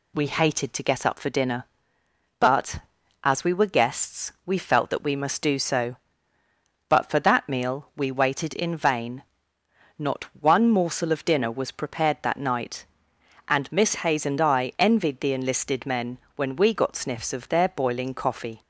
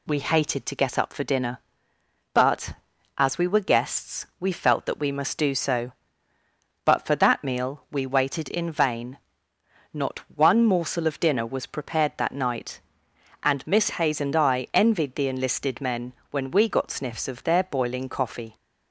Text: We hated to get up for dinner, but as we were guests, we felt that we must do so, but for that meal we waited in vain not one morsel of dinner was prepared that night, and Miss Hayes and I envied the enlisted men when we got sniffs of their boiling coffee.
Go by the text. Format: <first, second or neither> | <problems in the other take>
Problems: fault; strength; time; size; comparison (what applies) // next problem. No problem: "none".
neither | pauses between "vain" and "not"; noticeable; the same in both // pauses between "men" and "when"; slight; the same in both